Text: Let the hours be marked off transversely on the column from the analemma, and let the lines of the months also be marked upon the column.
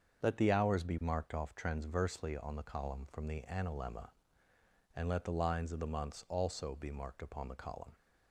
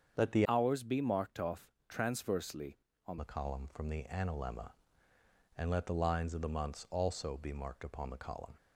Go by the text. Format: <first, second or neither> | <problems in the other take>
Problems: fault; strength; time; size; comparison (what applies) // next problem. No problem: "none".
first | starts louder than the rest; strong; until 1.2 s; 7 dB; also in the first // changes voice from "hours" to "on"; from 0.4 to 3.1 s; 2.7 s long // pauses between "off" and "transversely"; slight; at 1.7 s; 0.18 s long